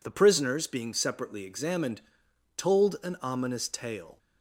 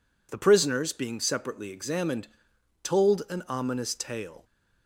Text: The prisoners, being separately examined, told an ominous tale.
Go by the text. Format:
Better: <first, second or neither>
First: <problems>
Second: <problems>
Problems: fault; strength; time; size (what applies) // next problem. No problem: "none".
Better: neither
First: none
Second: none